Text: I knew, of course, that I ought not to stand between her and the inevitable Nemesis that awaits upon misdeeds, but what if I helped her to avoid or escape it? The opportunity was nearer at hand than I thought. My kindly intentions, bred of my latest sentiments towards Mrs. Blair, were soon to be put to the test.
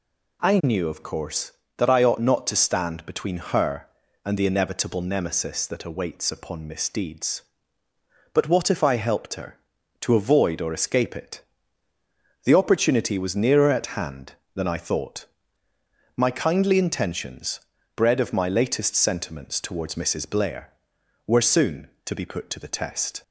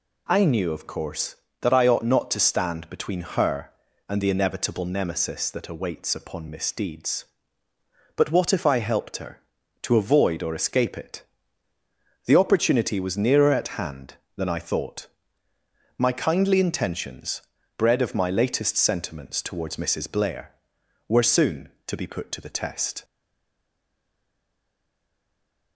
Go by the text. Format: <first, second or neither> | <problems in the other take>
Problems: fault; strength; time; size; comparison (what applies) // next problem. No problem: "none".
first | stays silent after the last word; strong; from 23.0 s on; 2.7 s long